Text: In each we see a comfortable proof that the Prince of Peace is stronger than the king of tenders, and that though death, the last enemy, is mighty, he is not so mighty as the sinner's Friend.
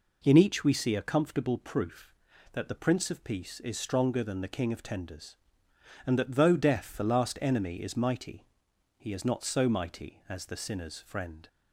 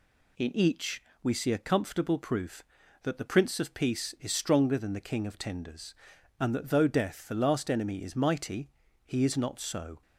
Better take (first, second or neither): first